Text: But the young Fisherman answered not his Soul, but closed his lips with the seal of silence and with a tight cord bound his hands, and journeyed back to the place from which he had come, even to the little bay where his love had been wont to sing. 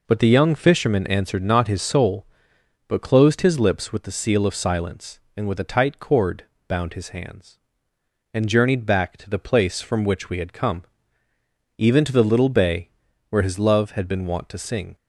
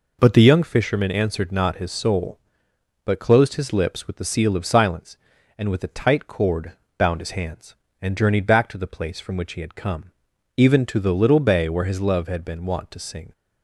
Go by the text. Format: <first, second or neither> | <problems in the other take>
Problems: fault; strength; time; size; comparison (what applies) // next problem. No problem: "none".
second | pauses between "cord" and "bound"; slight; at 6.4 s; 0.22 s long; slight in the second // says "we" for "he"; at 10.2 s // pauses between "bay" and "where"; at 12.8 s; 0.40 s long